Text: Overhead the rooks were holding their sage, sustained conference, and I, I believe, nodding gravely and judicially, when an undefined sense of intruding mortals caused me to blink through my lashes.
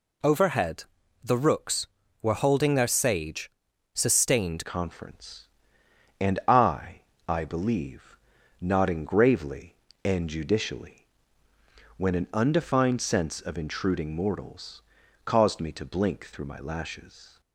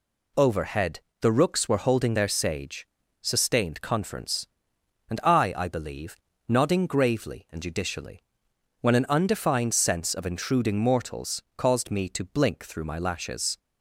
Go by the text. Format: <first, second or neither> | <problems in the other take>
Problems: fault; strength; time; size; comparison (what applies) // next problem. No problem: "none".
second | pauses between "Overhead" and "the"; at 0.8 s; 0.40 s long; slight in the second // changes voice at "conference"; from 4.6 s on; 12.8 s long // pauses between "mortals" and "caused"; at 14.8 s; 0.42 s long